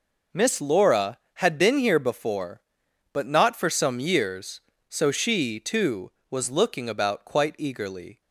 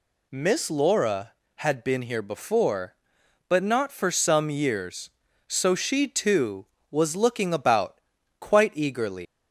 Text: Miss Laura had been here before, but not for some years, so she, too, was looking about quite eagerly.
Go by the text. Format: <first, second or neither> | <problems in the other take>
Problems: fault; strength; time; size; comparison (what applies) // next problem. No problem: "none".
first | pauses between "about" and "quite"; at 8.0 s; 0.40 s long // leaves "eagerly" unfinished; at 9.2 s; 115 ms